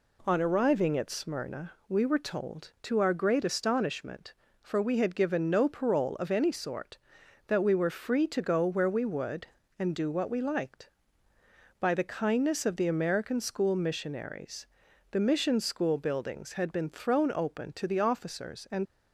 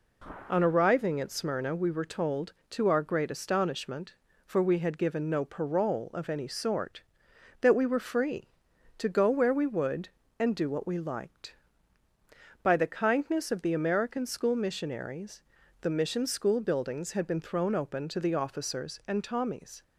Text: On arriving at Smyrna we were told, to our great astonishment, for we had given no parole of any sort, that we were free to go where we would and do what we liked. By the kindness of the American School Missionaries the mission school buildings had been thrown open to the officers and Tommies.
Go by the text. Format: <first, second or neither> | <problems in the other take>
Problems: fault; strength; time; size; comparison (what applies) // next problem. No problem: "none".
second | pauses between "Smyrna" and "we"; slight; at 1.7 s; 0.16 s long // pauses between "Missionaries" and "the"; at 14.6 s; 0.44 s long; also in the second // stops before "Tommies"; at 18.8 s